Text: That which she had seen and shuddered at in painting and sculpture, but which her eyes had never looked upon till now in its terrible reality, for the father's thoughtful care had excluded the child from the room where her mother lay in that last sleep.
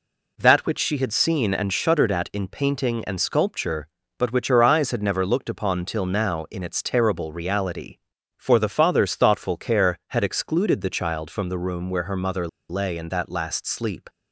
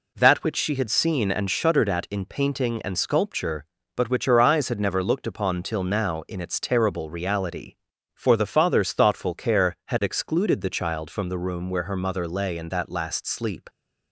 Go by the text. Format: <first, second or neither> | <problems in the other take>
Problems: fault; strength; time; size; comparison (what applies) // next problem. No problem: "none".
second | pauses between "mother" and "lay"; slight; at 12.4 s; 0.22 s long